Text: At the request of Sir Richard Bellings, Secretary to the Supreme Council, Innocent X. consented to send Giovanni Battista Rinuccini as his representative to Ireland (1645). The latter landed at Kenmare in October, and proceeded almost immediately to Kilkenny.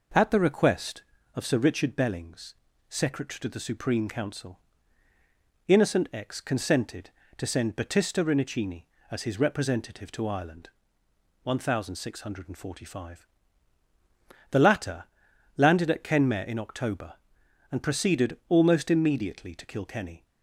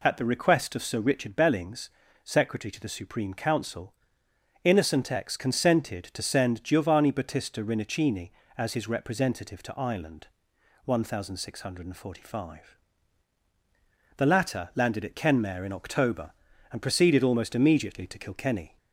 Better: second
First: skips "Giovanni"; at 7.7 s // pauses between "latter" and "landed"; noticeable; at 15.0 s; 0.50 s long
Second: none

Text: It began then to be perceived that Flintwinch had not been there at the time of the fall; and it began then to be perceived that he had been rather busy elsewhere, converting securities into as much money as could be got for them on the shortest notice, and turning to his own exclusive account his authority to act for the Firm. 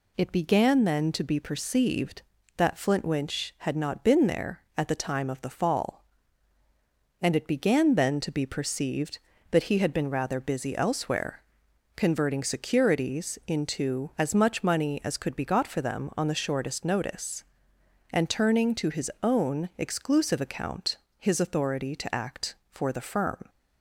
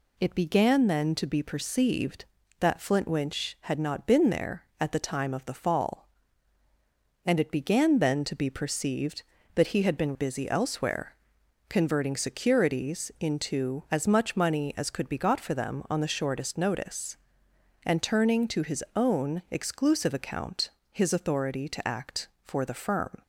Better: first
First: pauses between "account" and "his"; slight; at 20.9 s; 0.22 s long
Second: skips "rather"; at 10.1 s // pauses between "account" and "his"; slight; at 20.6 s; 0.22 s long

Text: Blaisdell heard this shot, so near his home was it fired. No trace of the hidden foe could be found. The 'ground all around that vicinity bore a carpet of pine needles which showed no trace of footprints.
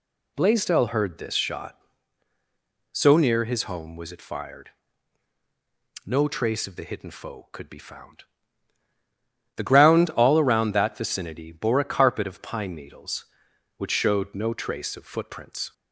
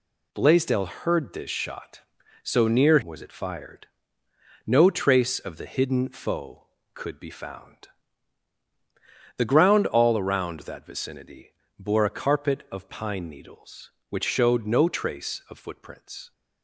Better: first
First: none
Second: skips "his home"; at 3.0 s // pauses between "vicinity" and "bore"; slight; at 11.5 s; 0.26 s long

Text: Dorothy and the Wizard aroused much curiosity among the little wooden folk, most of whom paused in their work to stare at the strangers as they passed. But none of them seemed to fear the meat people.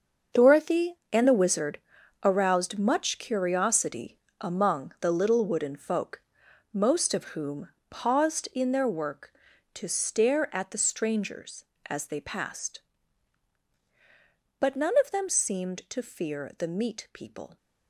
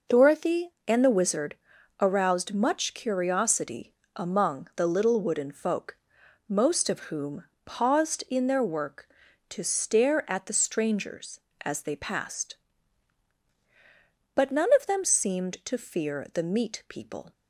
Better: second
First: gets quieter; strong; throughout; 12 dB // pauses between "Wizard" and "aroused"; at 1.7 s; 0.44 s long // pauses between "curiosity" and "among"; slight; at 4.1 s; 0.24 s long // pauses between "whom" and "paused"; slight; at 7.6 s; 0.22 s long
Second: pauses between "Wizard" and "aroused"; at 1.5 s; 0.44 s long // pauses between "curiosity" and "among"; slight; at 3.9 s; 0.24 s long // pauses between "whom" and "paused"; slight; at 7.4 s; 0.22 s long

